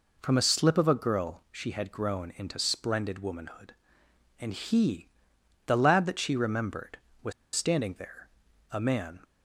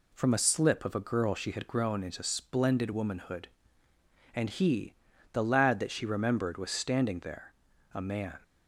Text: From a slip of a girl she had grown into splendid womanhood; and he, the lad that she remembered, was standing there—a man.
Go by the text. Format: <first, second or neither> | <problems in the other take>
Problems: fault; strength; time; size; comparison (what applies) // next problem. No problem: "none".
second | pauses between "was" and "standing"; slight; at 7.3 s; 0.23 s long